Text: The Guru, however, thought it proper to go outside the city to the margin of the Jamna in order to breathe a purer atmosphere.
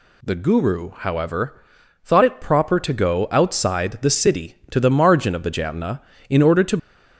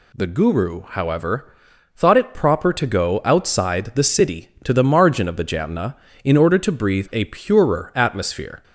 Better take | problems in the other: second | stops before "breathe a purer atmosphere"; at 6.7 s

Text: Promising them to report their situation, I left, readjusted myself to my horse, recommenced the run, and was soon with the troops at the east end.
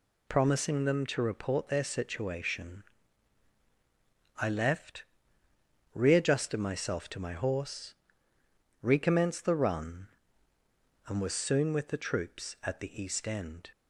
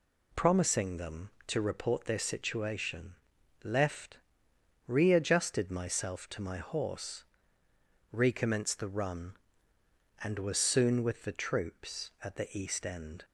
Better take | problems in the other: first | skips "I"; at 3.3 s

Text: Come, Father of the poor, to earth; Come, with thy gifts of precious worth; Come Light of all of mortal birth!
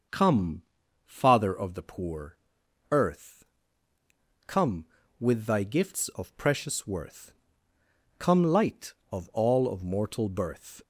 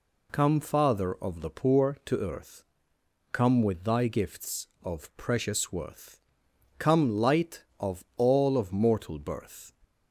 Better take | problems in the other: second | starts louder than the rest; noticeable; until 1.5 s; 6 dB // skips "to"; at 2.6 s

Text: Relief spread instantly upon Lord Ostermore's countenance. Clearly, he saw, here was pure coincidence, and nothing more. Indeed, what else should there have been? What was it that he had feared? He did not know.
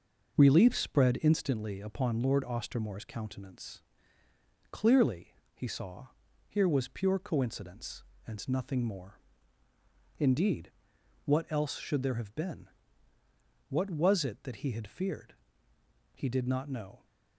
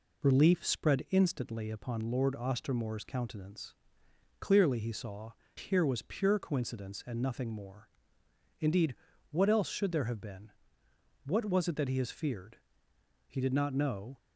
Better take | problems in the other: first | says "has" for "had"; at 11.9 s

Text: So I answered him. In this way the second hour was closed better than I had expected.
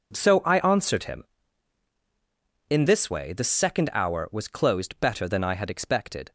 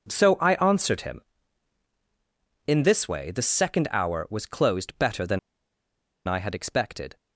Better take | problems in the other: first | pauses between "than" and "I"; noticeable; at 5.3 s; 0.88 s long

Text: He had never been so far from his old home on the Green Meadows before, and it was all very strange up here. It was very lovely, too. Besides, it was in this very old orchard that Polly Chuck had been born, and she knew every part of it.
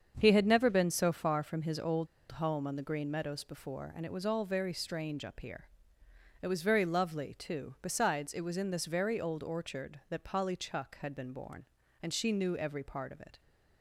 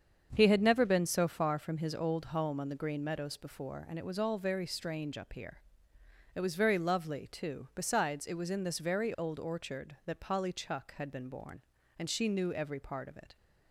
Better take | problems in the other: second | starts louder than the rest; until 1.1 s; 7 dB; also in the second // pauses between "old" and "home"; slight; at 2.0 s; 0.25 s long

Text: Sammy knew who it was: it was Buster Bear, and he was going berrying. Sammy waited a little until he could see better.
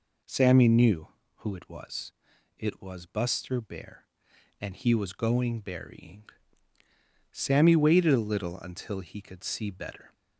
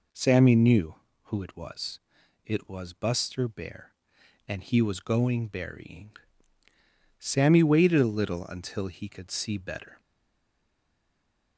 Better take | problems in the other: first | stays silent after the last word; noticeable; from 9.9 s on; 1.6 s long

